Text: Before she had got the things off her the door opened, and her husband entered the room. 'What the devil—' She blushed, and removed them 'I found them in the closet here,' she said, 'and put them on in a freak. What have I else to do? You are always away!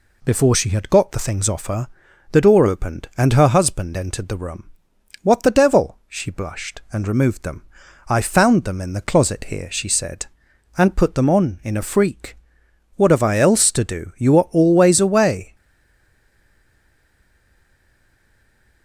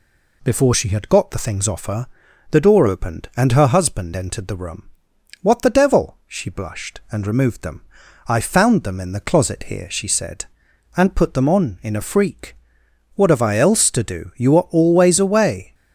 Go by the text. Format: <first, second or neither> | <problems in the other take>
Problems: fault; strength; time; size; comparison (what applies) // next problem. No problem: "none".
second | pauses between "her" and "the"; at 1.8 s; 0.44 s long; also in the second // pauses between "them" and "I"; at 7.6 s; 0.44 s long; also in the second // stays silent after the last word; strong; from 15.5 s on; 3.3 s long